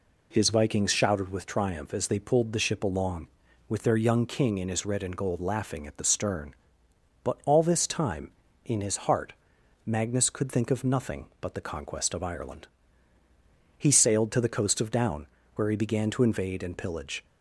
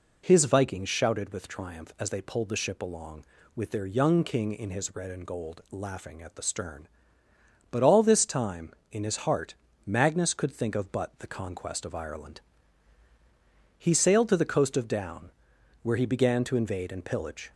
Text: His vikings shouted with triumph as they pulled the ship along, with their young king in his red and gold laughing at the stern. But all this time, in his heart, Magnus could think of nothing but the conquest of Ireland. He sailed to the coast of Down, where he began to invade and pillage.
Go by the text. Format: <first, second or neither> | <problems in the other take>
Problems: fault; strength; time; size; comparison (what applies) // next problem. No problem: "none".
first | skips "nothing"; at 10.9 s